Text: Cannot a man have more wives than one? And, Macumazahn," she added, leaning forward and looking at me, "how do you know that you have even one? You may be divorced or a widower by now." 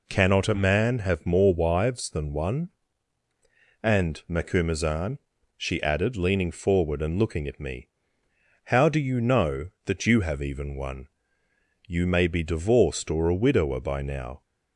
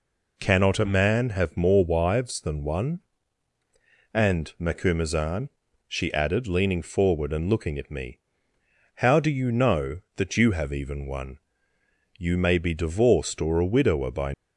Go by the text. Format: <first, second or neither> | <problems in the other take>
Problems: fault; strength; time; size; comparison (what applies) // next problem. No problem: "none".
first | stops before "now"; at 14.3 s